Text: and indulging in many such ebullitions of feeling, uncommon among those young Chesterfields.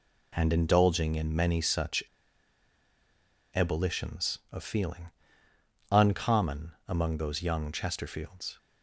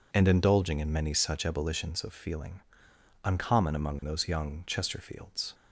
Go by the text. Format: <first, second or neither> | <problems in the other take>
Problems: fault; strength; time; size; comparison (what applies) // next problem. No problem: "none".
second | pauses between "such" and "ebullitions"; strong; at 2.0 s; 1.4 s long // pauses between "uncommon" and "among"; slight; at 6.7 s; 0.16 s long